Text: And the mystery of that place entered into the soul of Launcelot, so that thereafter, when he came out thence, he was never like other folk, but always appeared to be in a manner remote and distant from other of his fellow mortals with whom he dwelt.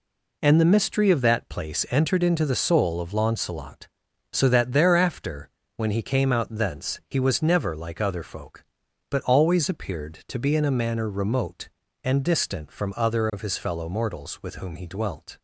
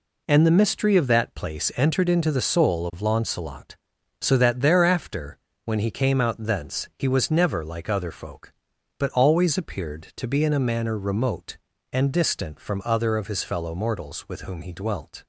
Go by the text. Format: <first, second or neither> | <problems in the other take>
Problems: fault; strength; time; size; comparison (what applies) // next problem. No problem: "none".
neither | none